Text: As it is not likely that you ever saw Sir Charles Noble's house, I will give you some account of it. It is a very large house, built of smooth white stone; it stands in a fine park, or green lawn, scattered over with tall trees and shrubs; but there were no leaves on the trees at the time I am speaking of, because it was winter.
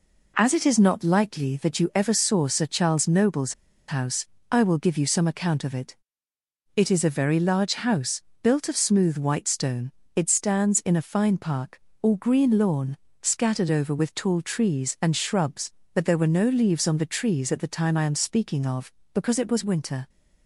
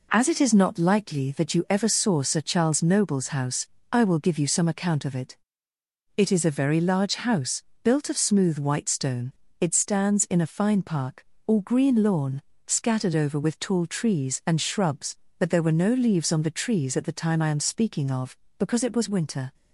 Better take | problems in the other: second | pauses between "Noble's" and "house"; slight; at 3.5 s; 0.35 s long

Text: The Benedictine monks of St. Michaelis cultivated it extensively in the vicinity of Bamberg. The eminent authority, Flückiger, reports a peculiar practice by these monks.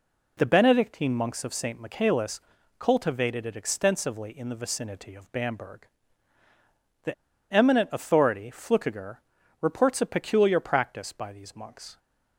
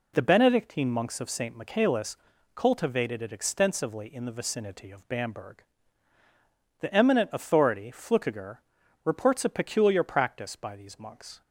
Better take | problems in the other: second | pauses between "Michaelis" and "cultivated"; at 2.3 s; 0.40 s long; also in the second // pauses between "The" and "eminent"; at 7.1 s; 0.39 s long

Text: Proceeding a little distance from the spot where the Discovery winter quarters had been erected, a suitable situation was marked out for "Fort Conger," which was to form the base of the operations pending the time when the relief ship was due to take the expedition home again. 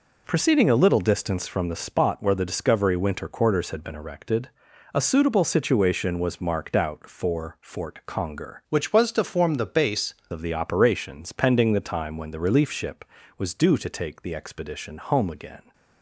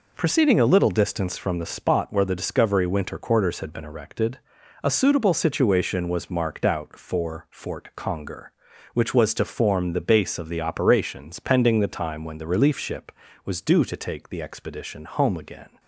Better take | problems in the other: second | changes voice from "which" to "base"; from 8.6 to 10.1 s; 1.5 s long

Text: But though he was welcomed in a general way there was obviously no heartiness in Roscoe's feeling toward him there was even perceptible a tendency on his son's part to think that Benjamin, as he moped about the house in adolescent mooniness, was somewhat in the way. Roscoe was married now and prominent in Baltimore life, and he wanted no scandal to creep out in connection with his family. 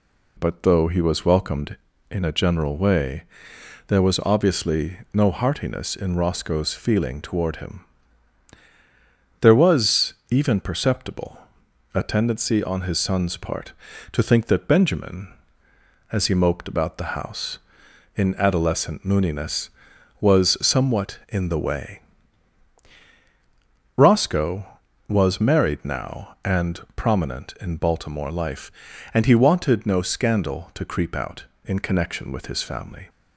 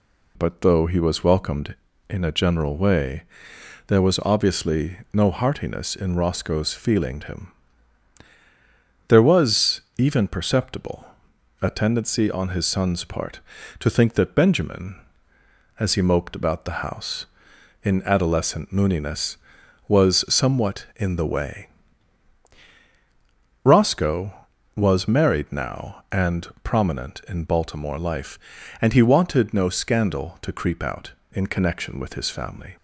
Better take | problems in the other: first | pauses between "way" and "there"; noticeable; at 3.2 s; 0.66 s long; noticeable in the first // pauses between "obviously" and "no"; slight; at 4.9 s; 0.16 s long; slight in the first // skips "toward"; at 7.2 s // pauses between "him" and "there"; strong; at 7.4 s; 1.5 s long; strong in the first // pauses between "was" and "even"; slight; at 9.7 s; 0.18 s long; slight in the first // pauses between "perceptible" and "a"; noticeable; at 11.0 s; 0.56 s long; noticeable in the first // pauses between "and" and "prominent"; slight; at 26.4 s; 0.16 s long; slight in the first

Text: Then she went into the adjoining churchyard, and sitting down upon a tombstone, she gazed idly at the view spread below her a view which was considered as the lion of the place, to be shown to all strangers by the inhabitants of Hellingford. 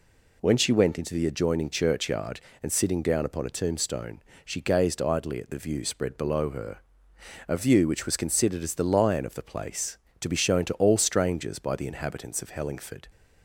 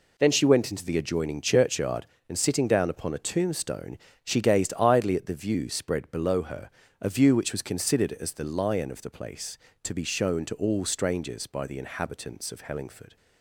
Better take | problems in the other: second | says "When" for "Then"; at 0.4 s // pauses between "her" and "a"; noticeable; at 6.7 s; 0.70 s long; slight in the second

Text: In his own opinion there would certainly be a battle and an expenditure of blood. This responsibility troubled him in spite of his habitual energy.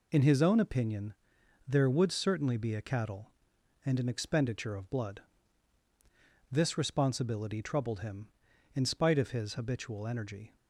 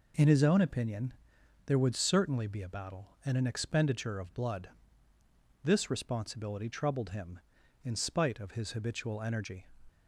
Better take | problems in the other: second | pauses between "opinion" and "there"; noticeable; at 1.1 s; 0.54 s long; noticeable in the second // says "cattle" for "battle"; at 2.8 s

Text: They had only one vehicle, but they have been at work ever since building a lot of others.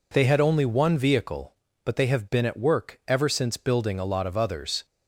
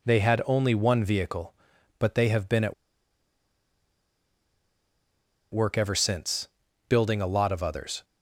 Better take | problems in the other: first | pauses between "at" and "work"; strong; at 2.7 s; 2.7 s long // pauses between "since" and "building"; at 6.4 s; 0.40 s long

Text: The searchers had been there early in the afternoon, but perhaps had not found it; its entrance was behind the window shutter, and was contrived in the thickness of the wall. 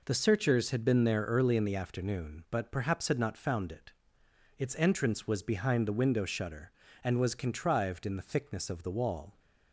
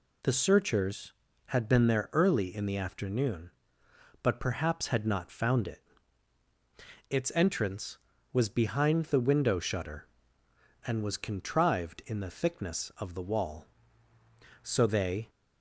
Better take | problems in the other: first | goes on to say "So they"; noticeable; from 14.6 s on; 0.68 s long

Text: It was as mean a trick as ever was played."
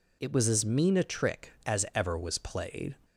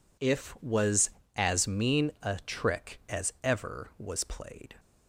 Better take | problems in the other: first | says "If" for "It"; at 0.1 s

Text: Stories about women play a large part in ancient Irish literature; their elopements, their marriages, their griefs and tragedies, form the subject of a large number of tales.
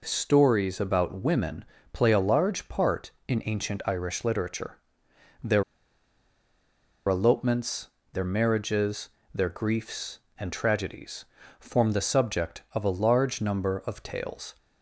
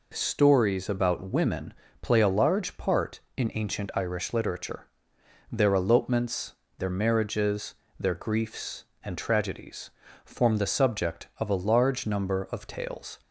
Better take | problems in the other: second | pauses between "women" and "play"; slight; at 1.6 s; 0.30 s long; slight in the second // pauses between "their" and "elopements"; strong; at 5.6 s; 1.4 s long

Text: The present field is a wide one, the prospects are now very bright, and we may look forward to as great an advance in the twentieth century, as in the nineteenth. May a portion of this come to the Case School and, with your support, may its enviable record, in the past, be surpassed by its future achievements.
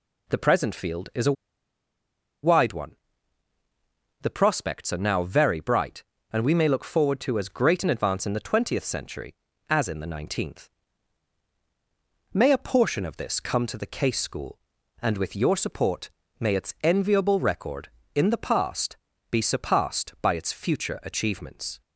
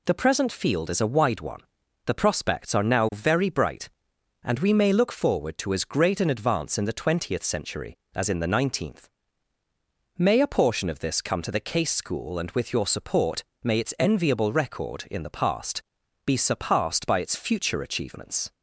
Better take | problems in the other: second | pauses between "a" and "wide"; at 1.3 s; 1.0 s long

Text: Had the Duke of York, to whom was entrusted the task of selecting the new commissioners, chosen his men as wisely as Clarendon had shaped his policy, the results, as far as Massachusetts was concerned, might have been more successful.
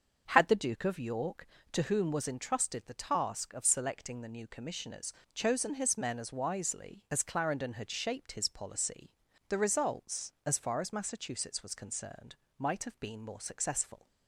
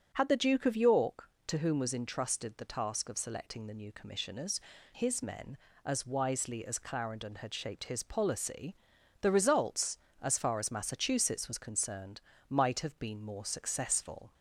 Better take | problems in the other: first | starts louder than the rest; until 1.1 s; 6 dB; also in the first // skips "chosen"; at 4.7 s

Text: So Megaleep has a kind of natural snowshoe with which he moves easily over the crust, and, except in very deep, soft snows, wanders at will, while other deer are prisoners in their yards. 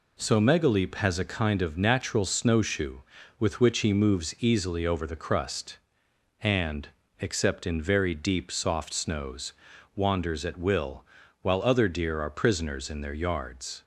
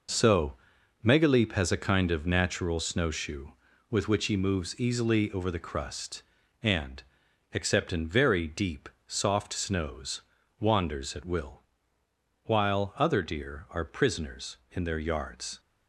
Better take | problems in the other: first | gets quieter; strong; throughout; 7.5 dB // pauses between "So" and "Megaleep"; noticeable; at 0.5 s; 0.50 s long

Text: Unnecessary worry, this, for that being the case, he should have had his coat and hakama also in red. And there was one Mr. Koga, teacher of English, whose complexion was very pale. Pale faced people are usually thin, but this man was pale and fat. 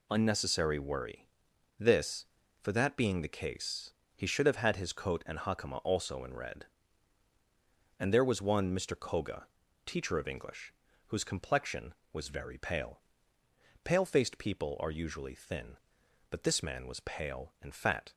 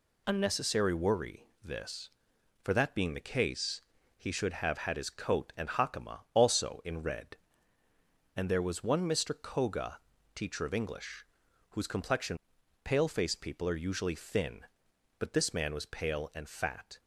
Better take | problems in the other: first | skips "was very pale"; at 12.6 s

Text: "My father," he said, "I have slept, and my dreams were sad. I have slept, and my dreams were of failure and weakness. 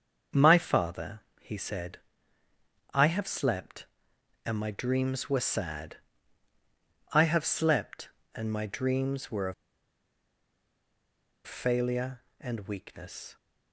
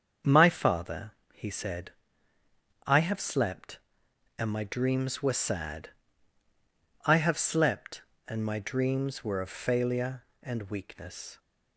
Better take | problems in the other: second | starts louder than the rest; until 1.5 s; 7 dB; also in the second // pauses between "of" and "failure"; strong; at 9.5 s; 1.9 s long

